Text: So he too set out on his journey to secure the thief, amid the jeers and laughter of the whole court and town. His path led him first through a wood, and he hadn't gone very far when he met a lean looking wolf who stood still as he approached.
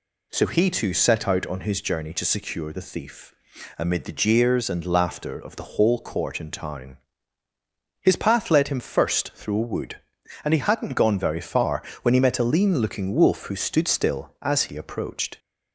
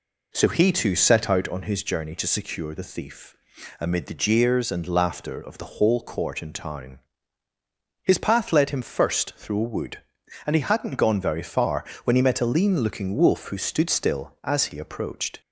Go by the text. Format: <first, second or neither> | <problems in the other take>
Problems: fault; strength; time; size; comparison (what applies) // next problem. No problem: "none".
first | starts louder than the rest; until 1.5 s; 3.5 dB // pauses between "far" and "when"; slight; at 11.8 s; 0.20 s long; slight in the first